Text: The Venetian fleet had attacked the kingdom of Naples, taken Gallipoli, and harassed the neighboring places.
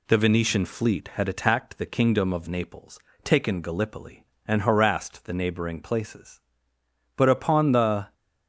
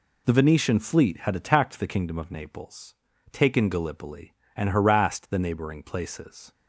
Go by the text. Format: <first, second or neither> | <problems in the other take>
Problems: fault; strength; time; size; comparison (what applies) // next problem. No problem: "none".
second | goes on to say "But upon the"; noticeable; from 7.1 s on; 0.98 s long